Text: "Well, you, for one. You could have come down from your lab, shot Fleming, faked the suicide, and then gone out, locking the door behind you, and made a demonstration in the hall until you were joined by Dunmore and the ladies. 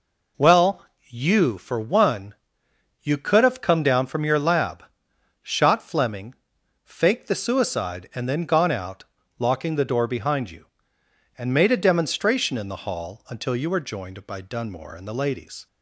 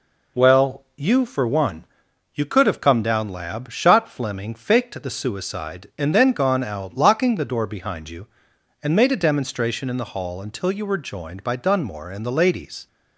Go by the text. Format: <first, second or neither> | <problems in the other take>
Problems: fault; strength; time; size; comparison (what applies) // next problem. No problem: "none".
first | skips "from your"; at 3.2 s